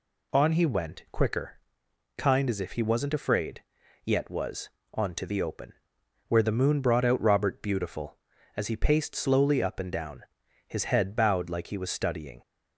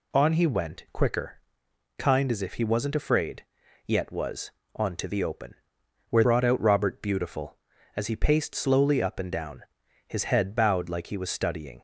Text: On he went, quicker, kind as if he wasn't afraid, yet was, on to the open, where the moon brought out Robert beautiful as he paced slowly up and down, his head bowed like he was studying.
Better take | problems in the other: first | skips "the moon"; at 6.2 s

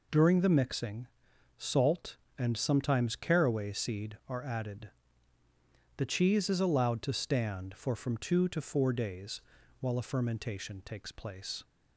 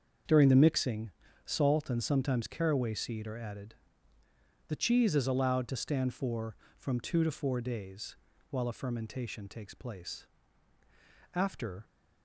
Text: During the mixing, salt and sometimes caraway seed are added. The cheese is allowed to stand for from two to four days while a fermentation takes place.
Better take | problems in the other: first | starts louder than the rest; until 1.6 s; 7 dB // pauses between "days" and "while"; slight; at 8.1 s; 0.34 s long; also in the first // goes on to say "After"; from 11.3 s on; 0.52 s long

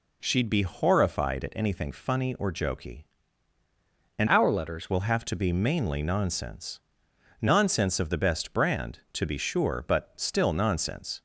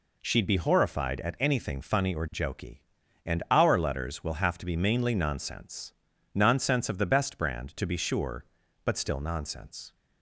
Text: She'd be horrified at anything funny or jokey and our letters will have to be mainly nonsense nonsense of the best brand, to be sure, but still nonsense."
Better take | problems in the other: second | changes voice from "our" to "letters"; from 4.2 to 4.9 s; 0.7 s long // pauses between "nonsense" and "nonsense"; noticeable; at 6.8 s; 0.60 s long; also in the second

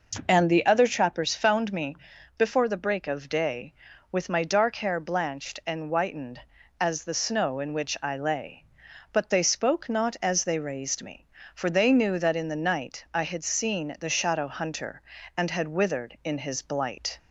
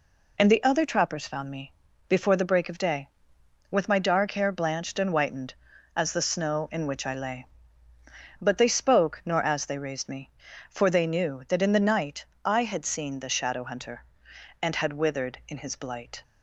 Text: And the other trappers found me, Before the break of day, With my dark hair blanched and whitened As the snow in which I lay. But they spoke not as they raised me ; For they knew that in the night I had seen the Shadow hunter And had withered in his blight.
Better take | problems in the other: first | says "nor" for "not"; at 9.2 s // pauses between "night" and "I"; slight; at 12.2 s; 0.22 s long

